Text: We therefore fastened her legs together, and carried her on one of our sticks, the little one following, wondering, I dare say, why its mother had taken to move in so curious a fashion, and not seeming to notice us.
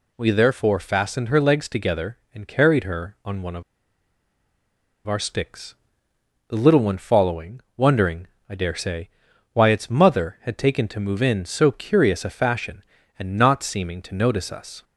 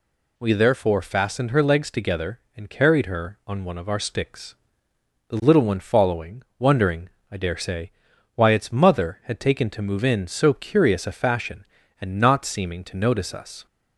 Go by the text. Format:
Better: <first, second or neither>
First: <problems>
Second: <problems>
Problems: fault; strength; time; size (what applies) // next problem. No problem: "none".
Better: second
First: pauses between "of" and "our"; strong; at 3.6 s; 1.4 s long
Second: none